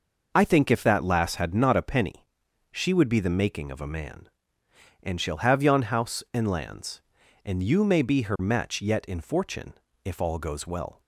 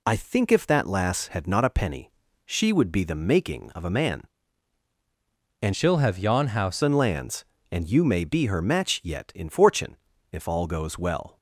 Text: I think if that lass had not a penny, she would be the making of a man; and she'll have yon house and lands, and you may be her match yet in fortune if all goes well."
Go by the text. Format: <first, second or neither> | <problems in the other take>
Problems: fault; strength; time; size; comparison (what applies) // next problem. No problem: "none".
first | changes voice from "she'll" to "house"; from 5.7 to 6.8 s; 1.1 s long // pauses between "fortune" and "if"; slight; at 9.9 s; 0.36 s long; slight in the first